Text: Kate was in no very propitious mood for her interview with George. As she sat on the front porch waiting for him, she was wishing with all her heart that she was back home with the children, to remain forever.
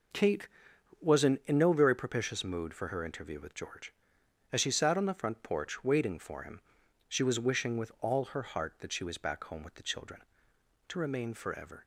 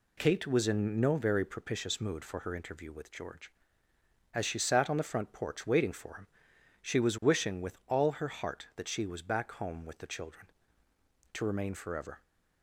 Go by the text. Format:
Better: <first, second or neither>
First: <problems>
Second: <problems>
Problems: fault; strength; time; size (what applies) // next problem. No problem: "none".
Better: second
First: says "in" twice; at 1.4 s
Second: none